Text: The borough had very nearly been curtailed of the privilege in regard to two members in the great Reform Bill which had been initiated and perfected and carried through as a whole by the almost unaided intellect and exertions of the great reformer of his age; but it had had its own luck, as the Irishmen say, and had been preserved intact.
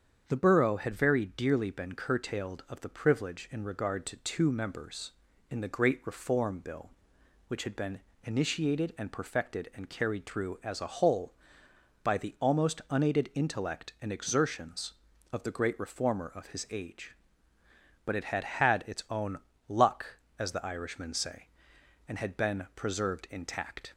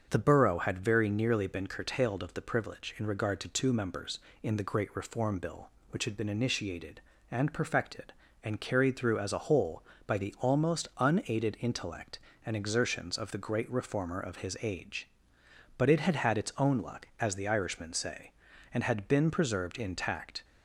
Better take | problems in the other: second | starts louder than the rest; strong; until 1.2 s; 7.5 dB; also in the second // says "dearly" for "nearly"; at 1.2 s // pauses between "been" and "initiated"; slight; at 8.0 s; 0.24 s long // pauses between "own" and "luck"; slight; at 19.3 s; 0.30 s long

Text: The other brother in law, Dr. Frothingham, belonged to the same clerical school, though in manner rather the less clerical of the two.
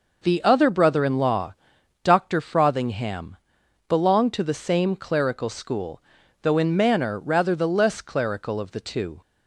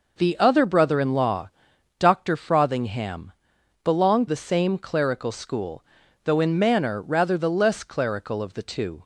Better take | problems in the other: first | skips "to"; at 4.2 s

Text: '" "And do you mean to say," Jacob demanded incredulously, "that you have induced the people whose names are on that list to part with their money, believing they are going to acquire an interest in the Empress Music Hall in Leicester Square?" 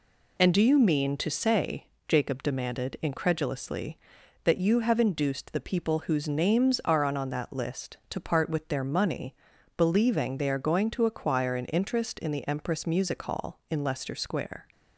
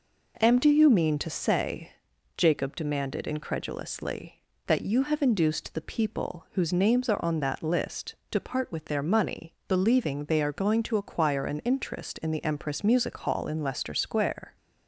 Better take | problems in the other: second | says "on" twice; at 7.1 s

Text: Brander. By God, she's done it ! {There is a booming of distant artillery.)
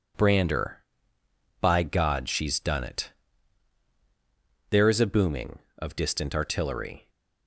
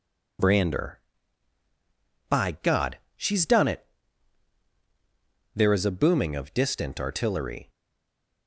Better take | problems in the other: first | stays silent after the last word; slight; from 7.6 s on; 0.8 s long

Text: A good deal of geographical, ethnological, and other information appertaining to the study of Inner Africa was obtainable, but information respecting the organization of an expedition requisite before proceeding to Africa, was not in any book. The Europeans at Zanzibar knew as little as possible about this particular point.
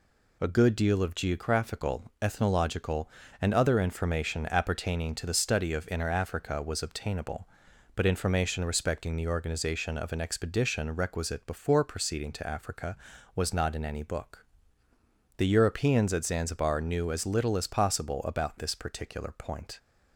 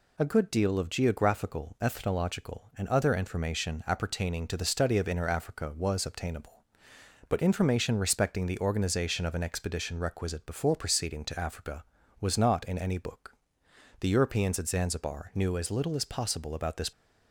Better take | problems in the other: first | stops before "particular point"; at 16.9 s

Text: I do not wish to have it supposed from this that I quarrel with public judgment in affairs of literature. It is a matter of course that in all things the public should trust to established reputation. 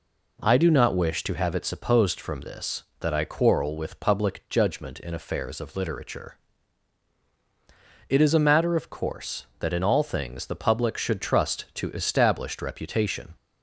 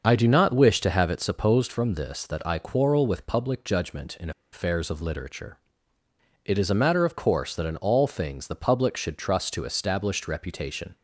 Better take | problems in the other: first | starts louder than the rest; until 1.0 s; 6.5 dB // pauses between "in" and "affairs"; slight; at 4.3 s; 0.22 s long

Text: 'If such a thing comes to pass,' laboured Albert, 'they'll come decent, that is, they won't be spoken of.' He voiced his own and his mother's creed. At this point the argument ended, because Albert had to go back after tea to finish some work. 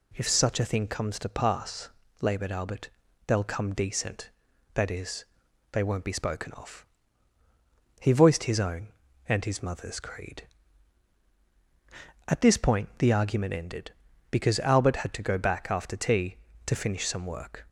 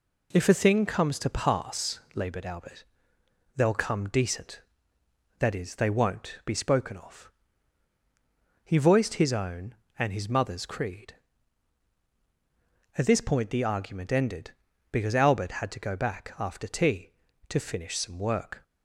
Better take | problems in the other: first | skips "such"; at 0.4 s

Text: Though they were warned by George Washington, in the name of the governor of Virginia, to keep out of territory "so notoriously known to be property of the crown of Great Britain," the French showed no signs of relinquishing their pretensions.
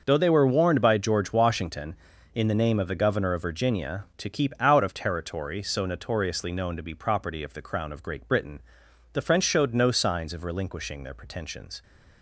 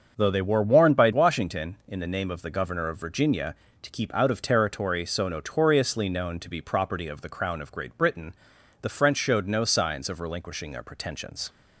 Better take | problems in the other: first | starts louder than the rest; until 1.1 s; 6.5 dB; also in the first // skips "George"; at 1.1 s

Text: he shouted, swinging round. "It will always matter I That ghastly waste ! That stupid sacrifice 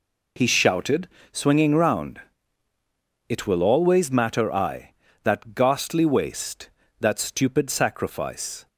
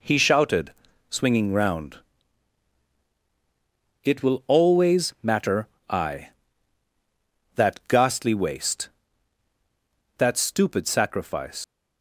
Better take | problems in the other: first | pauses between "matter" and "I"; slight; at 5.6 s; 0.20 s long // leaves "sacrifice" unfinished; at 11.6 s; 115 ms

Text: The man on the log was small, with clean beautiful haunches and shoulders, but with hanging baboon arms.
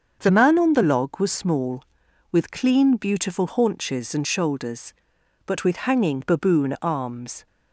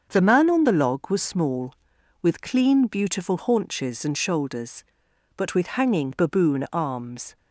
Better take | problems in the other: neither | starts louder than the rest; the same in both

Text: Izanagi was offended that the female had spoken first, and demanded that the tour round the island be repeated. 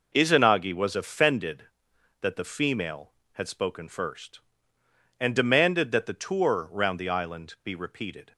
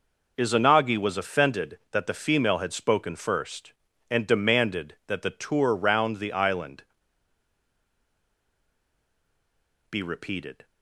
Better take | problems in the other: first | pauses between "island" and "be"; strong; at 6.8 s; 3.0 s long

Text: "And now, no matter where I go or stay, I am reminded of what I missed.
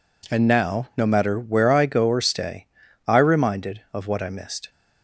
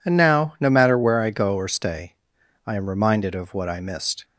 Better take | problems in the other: second | skips "am"; at 3.1 s

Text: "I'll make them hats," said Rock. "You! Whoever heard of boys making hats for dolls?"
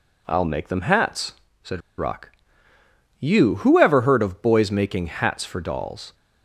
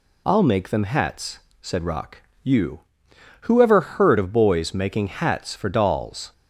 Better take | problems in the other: second | pauses between "said" and "Rock"; slight; at 1.8 s; 0.19 s long

